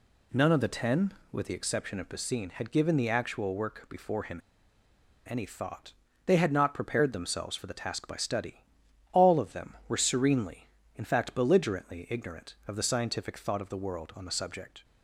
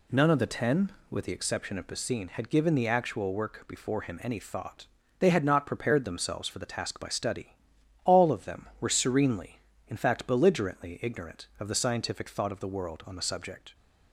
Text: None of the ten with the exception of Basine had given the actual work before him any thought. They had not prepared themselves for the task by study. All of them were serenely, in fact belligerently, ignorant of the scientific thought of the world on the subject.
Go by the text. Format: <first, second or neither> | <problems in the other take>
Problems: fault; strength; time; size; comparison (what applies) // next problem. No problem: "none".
second | pauses between "him" and "any"; noticeable; at 4.3 s; 0.88 s long